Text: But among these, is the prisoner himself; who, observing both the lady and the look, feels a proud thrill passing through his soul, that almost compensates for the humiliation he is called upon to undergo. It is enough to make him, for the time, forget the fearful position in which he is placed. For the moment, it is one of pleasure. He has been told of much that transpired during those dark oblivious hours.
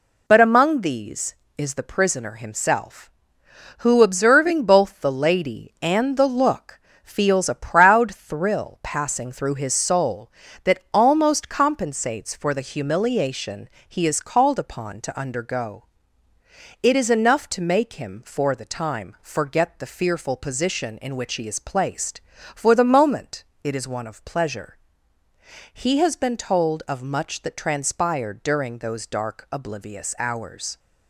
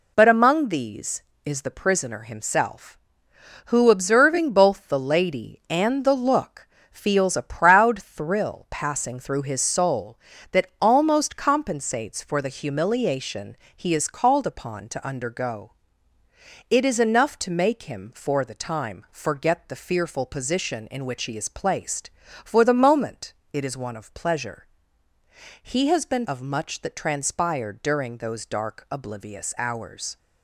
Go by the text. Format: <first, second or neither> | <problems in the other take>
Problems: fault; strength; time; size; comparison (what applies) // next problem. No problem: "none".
first | pauses between "humiliation" and "he"; slight; at 13.5 s; 0.20 s long; slight in the first // skips "told"; at 26.2 s